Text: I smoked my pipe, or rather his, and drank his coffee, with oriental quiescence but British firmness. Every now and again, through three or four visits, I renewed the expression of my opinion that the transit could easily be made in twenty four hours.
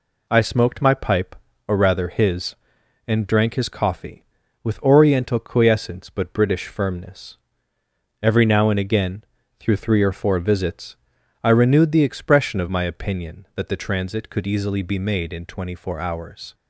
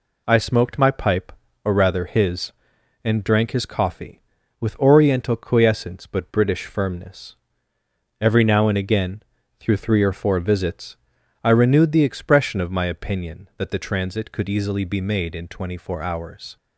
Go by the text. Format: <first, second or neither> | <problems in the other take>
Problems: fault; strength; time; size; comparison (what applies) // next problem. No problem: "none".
neither | none